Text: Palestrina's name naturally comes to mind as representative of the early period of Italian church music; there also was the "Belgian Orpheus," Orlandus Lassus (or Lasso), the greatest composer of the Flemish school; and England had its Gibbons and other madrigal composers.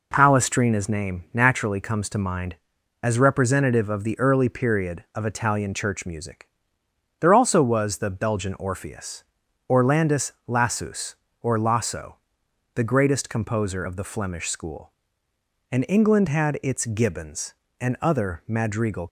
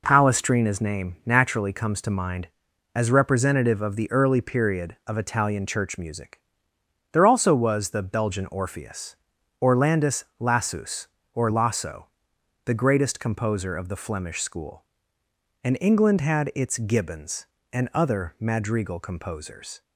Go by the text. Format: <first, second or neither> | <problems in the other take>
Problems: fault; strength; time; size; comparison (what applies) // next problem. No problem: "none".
second | stops before "composers"; at 19.0 s